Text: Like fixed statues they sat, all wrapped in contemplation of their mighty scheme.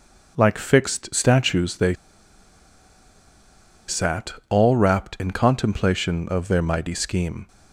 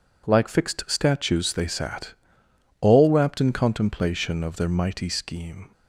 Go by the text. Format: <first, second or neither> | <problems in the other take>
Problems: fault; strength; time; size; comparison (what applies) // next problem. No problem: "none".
second | pauses between "they" and "sat"; strong; at 1.9 s; 1.9 s long